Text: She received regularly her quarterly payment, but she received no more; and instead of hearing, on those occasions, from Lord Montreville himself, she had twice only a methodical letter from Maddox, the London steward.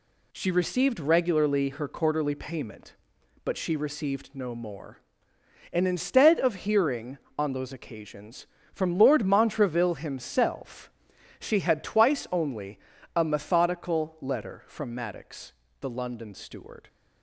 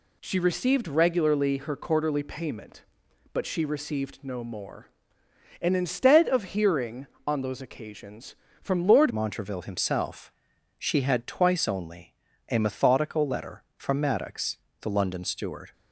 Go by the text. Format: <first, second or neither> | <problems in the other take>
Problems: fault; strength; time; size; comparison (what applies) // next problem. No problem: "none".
first | changes voice at "Montreville"; from 9.1 s on; 6.6 s long // pauses between "only" and "a"; slight; at 12.1 s; 0.36 s long; slight in the first